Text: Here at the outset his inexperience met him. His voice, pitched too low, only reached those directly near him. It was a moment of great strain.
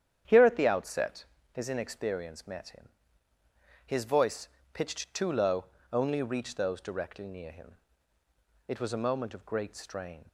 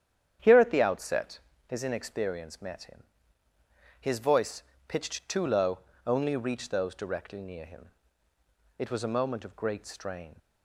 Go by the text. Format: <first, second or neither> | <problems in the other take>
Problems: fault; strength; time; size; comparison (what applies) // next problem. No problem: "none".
neither | starts louder than the rest; strong; the same in both // pauses between "outset" and "his"; slight; the same in both